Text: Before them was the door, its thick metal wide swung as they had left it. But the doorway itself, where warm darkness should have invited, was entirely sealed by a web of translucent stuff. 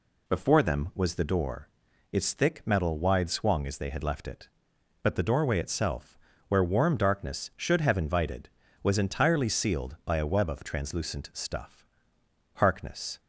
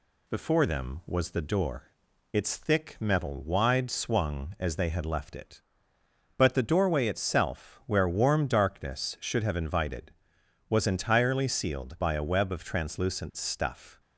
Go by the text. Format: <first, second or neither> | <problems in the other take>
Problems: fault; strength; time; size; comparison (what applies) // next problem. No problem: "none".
second | goes on to say "Harkness"; noticeable; from 12.5 s on; 0.64 s long